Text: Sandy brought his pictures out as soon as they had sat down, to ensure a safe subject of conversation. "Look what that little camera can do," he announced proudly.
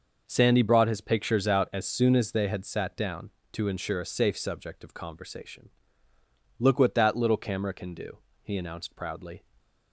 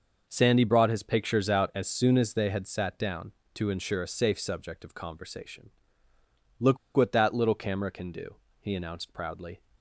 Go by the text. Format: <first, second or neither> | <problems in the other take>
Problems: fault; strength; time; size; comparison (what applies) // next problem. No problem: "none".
first | pauses between "Look" and "what"; slight; at 6.7 s; 0.17 s long